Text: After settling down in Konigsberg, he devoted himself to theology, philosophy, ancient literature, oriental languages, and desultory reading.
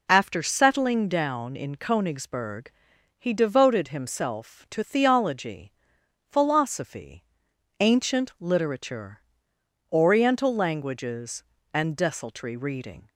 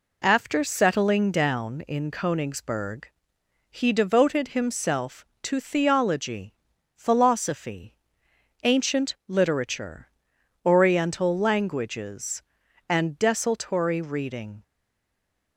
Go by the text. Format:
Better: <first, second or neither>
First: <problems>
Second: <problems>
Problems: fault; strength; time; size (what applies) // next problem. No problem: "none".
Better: first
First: none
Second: stays silent after the last word; slight; from 14.6 s on; 0.9 s long